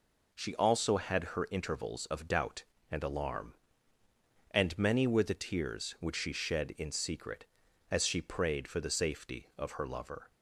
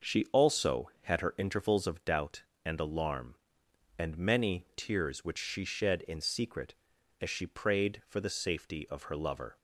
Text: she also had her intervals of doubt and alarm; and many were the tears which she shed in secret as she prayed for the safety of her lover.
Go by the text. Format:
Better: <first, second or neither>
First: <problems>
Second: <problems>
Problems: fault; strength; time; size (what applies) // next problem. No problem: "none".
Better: first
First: none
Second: skips "were the"; at 4.6 s